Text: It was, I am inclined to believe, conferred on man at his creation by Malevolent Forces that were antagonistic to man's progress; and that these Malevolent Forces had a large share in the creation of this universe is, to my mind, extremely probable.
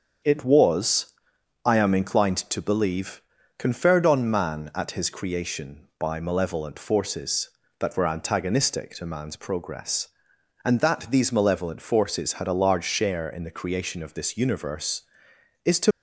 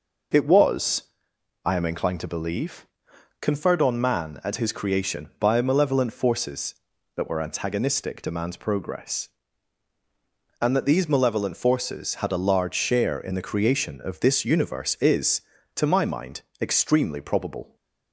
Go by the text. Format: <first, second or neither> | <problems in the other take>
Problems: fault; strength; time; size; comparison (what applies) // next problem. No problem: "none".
second | starts louder than the rest; strong; until 1.8 s; 7.5 dB // stops before "my mind extremely probable"; at 15.9 s